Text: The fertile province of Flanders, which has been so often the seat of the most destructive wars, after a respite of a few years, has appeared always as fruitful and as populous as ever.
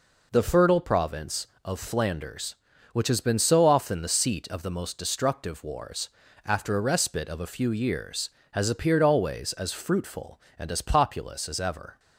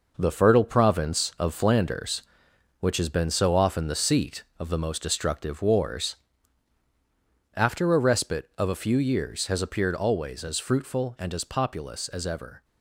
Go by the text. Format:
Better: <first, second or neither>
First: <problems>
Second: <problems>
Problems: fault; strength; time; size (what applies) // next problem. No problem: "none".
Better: first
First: none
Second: gets quieter; strong; throughout; 7.5 dB